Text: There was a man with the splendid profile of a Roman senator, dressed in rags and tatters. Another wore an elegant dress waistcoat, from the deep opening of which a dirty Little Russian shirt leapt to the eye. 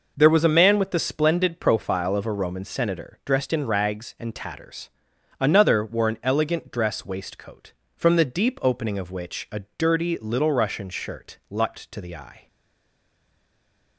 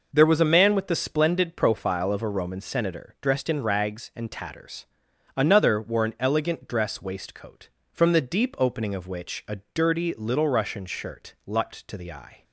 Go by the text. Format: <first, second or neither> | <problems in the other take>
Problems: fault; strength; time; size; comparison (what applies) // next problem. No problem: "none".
second | stays silent after the last word; noticeable; from 12.4 s on; 1.5 s long